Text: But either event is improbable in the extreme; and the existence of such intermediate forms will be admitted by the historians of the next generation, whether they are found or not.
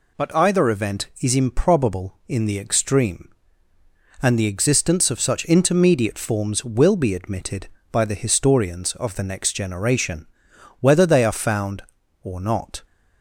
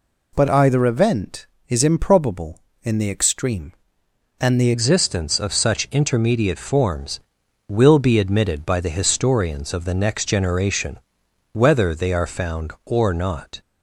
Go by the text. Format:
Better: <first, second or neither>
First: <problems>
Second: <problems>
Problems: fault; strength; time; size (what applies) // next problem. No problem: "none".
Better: first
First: none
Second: changes voice at "existence"; from 4.7 s on; 8.9 s long